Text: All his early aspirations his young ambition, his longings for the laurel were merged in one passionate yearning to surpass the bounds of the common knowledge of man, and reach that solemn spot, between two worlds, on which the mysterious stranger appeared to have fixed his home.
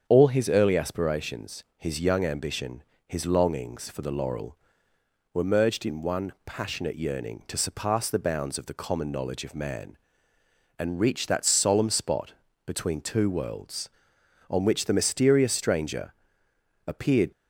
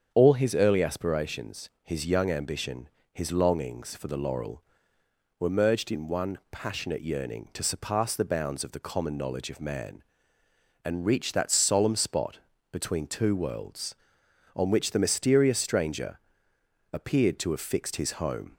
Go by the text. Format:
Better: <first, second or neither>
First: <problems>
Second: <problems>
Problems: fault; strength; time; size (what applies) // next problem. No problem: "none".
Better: second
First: starts louder than the rest; strong; until 1.0 s; 7.5 dB // pauses between "aspirations" and "his"; slight; at 1.6 s; 0.16 s long // pauses between "stranger" and "appeared"; noticeable; at 16.1 s; 0.74 s long // stops before "to have fixed his home"; at 17.3 s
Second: starts louder than the rest; strong; until 1.1 s; 7.5 dB // pauses between "aspirations" and "his"; slight; at 1.6 s; 0.16 s long // pauses between "stranger" and "appeared"; noticeable; at 16.1 s; 0.74 s long